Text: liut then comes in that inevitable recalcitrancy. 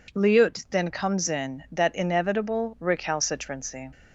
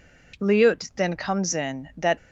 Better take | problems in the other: first | stops before "inevitable recalcitrancy"; at 2.1 s

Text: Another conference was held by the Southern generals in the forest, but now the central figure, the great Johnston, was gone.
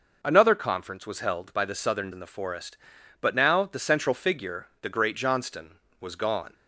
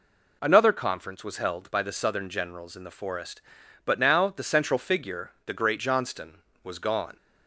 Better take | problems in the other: second | skips "generals"; at 2.1 s

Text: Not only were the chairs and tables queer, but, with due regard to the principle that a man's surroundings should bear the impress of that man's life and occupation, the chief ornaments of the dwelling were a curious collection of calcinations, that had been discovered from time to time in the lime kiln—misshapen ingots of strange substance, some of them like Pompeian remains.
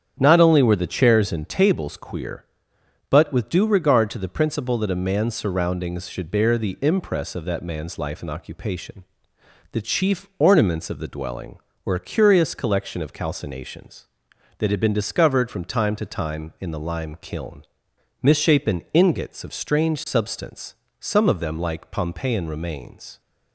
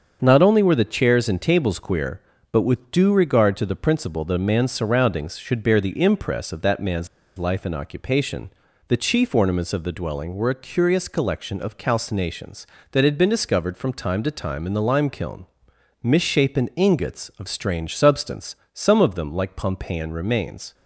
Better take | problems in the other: first | starts louder than the rest; until 1.2 s; 7 dB; strong in the first // pauses between "man's" and "life"; slight; at 7.0 s; 0.29 s long

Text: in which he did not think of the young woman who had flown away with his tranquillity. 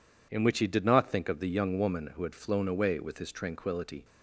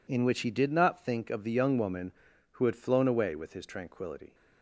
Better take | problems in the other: neither | none

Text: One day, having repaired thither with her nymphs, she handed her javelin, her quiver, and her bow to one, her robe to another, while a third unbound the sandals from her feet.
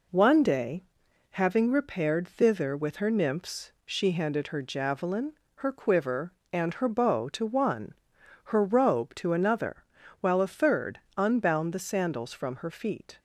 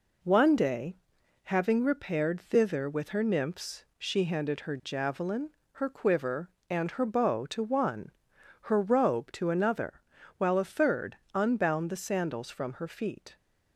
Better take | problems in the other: neither | pauses between "third" and "unbound"; slight; the same in both

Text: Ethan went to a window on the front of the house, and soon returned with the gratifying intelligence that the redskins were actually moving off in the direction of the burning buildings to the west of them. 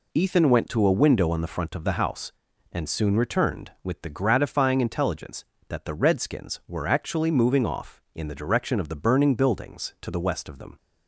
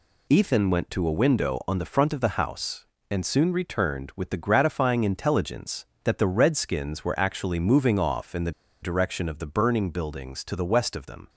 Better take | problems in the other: first | pauses between "the" and "direction"; slight; at 8.5 s; 0.30 s long

